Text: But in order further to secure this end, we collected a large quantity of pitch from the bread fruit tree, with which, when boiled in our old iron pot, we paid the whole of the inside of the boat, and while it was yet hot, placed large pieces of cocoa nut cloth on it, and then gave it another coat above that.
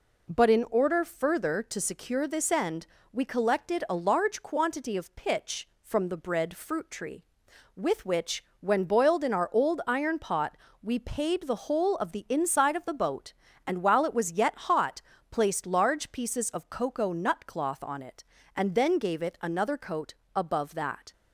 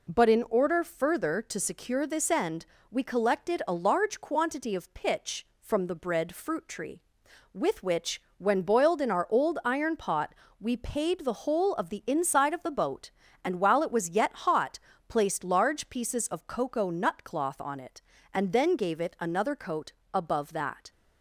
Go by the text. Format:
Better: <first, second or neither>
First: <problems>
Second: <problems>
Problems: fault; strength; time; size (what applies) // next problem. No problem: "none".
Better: neither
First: pauses between "coat" and "above"; slight; at 20.1 s; 0.22 s long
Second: pauses between "coat" and "above"; slight; at 19.9 s; 0.22 s long